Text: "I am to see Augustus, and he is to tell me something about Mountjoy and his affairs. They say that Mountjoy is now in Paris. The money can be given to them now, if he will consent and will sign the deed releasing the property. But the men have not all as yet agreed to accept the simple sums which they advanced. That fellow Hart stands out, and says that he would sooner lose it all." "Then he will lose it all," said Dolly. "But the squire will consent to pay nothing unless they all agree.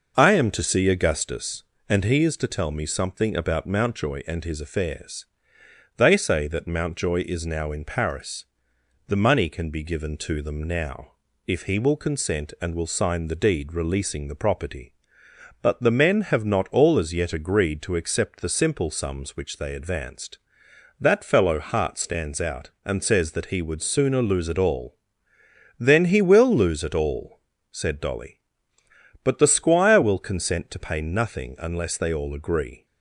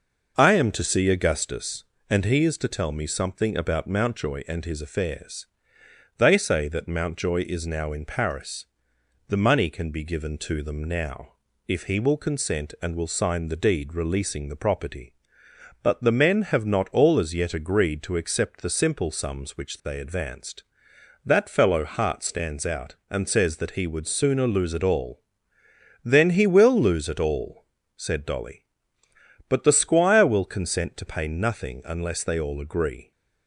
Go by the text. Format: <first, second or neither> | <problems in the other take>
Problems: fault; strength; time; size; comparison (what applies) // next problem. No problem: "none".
neither | none